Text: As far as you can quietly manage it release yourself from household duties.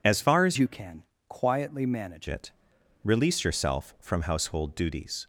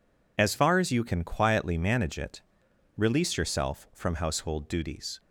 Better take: second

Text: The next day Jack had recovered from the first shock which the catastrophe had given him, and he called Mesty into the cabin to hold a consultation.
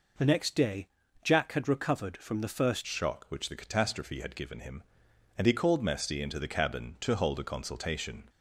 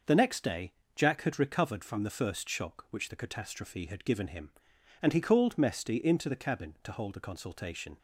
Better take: second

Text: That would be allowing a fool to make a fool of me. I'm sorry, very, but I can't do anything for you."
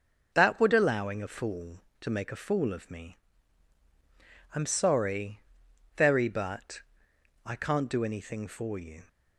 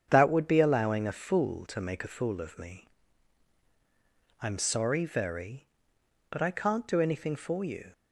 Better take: second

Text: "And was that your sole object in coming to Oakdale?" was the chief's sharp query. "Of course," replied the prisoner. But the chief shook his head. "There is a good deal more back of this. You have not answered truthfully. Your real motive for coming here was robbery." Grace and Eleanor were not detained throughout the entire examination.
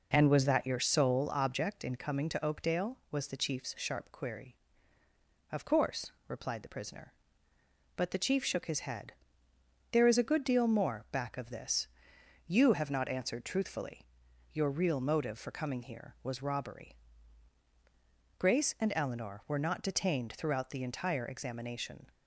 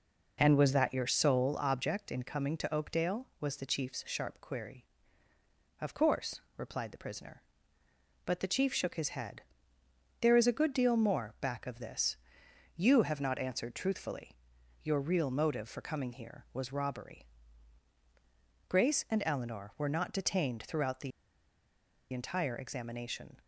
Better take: first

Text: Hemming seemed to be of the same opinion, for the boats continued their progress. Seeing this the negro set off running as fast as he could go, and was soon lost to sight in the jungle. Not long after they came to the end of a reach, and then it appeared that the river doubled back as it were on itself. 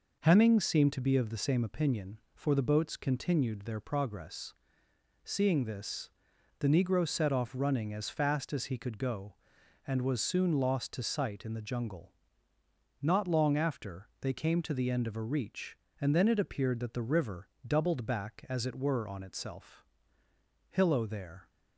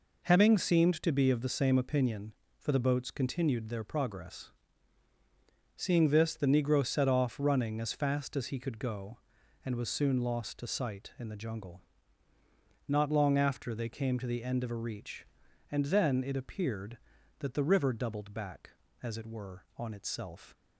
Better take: second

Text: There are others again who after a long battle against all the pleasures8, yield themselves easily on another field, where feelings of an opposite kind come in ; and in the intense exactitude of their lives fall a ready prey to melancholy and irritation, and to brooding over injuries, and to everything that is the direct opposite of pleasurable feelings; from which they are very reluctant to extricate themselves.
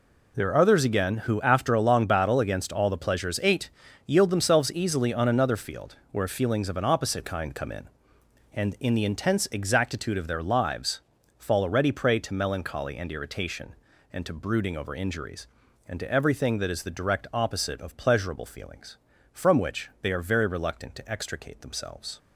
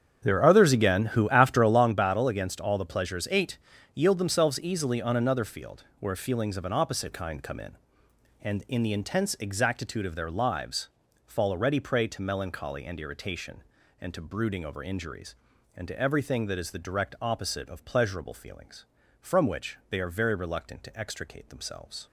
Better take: first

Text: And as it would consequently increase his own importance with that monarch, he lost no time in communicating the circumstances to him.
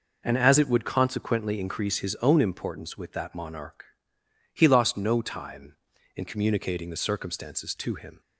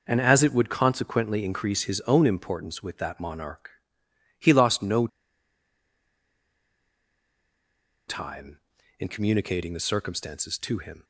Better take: first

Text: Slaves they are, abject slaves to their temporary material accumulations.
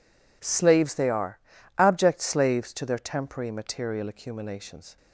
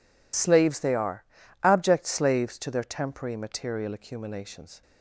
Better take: first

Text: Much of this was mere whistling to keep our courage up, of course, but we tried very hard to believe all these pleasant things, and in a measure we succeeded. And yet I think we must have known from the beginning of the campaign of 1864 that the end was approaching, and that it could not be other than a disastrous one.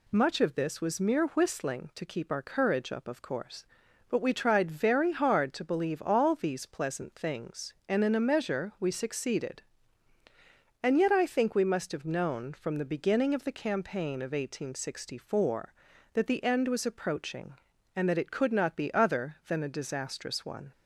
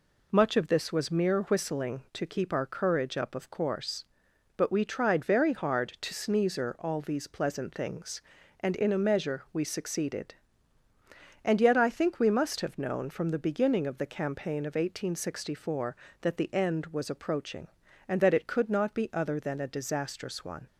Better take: first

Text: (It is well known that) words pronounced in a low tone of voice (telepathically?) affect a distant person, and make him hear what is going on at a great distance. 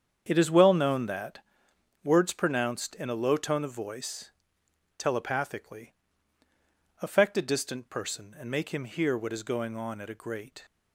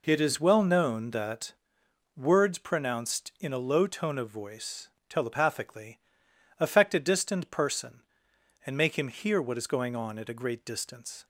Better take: second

